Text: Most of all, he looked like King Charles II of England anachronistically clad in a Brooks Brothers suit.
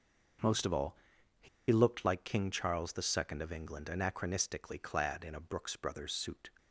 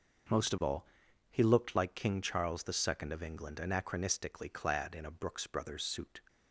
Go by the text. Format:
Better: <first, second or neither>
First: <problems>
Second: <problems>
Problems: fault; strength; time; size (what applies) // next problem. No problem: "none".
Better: second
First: starts louder than the rest; noticeable; until 2.1 s; 6 dB // pauses between "he" and "looked"; slight; at 1.4 s; 0.22 s long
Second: starts louder than the rest; until 1.7 s; 6 dB